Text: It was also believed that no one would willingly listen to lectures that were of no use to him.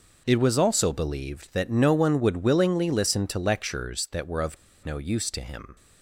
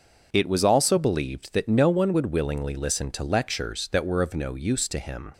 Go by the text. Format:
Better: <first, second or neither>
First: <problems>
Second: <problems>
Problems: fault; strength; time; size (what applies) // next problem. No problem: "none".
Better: second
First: pauses between "of" and "no"; slight; at 4.5 s; 0.26 s long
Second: none